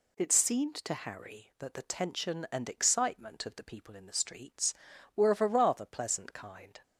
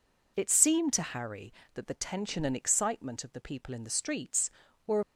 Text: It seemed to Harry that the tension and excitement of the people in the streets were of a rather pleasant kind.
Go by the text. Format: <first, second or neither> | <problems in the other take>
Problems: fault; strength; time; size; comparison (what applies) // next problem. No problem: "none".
first | stops before "of a rather pleasant kind"; at 5.0 s